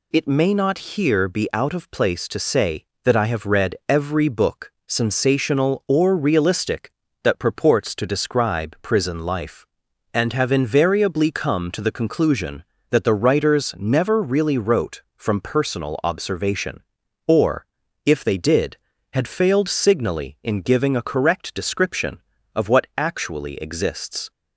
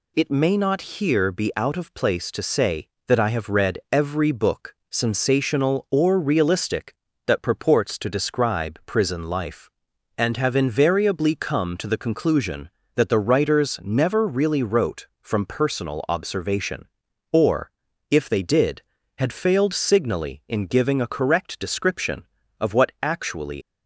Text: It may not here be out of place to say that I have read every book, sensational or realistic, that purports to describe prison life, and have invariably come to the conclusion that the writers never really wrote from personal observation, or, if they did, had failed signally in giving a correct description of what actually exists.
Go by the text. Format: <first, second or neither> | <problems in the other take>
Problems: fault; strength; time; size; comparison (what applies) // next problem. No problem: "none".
first | stops before "exists"; at 23.6 s